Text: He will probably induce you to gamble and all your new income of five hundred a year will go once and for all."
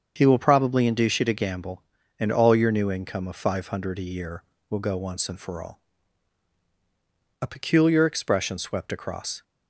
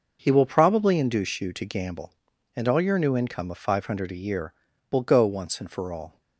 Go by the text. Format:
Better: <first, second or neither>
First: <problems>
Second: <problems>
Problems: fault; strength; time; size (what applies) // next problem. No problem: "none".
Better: second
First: starts louder than the rest; until 1.1 s; 7 dB // goes on to say "A peculiar expression swept across"; strong; from 7.4 s on; 2.0 s long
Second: none